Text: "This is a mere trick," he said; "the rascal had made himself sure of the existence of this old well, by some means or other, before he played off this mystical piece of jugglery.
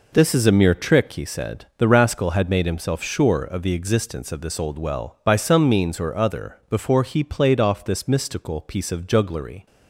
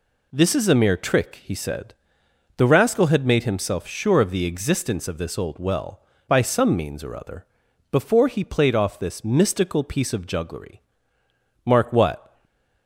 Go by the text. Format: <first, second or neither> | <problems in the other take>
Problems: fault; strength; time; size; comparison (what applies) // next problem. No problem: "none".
first | goes on to say "Mark what"; noticeable; from 11.6 s on; 0.68 s long // stays silent after the last word; slight; from 12.2 s on; 0.6 s long